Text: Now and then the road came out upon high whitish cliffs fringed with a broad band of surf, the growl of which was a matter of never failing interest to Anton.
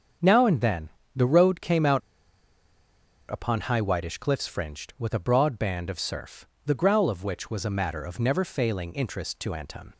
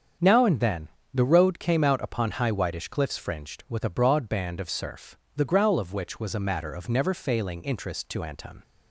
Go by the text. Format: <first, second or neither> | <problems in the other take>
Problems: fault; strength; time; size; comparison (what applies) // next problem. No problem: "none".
second | starts louder than the rest; strong; until 1.4 s; 7.5 dB; strong in the second // pauses between "then" and "the"; slight; at 0.8 s; 0.26 s long; slight in the second // pauses between "out" and "upon"; strong; at 2.0 s; 1.3 s long